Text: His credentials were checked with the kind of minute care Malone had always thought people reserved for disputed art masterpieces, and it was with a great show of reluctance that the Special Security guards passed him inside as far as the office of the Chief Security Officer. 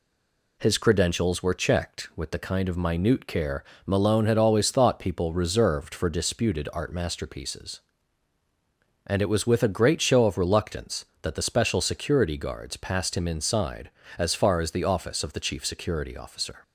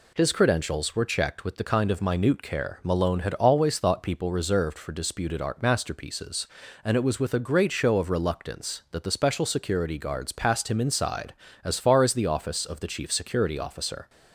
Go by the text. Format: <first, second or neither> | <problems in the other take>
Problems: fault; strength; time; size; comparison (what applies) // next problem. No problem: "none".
second | stays silent before the first word; slight; until 0.5 s; 0.5 s long // pauses between "care" and "Malone"; slight; at 3.6 s; 0.22 s long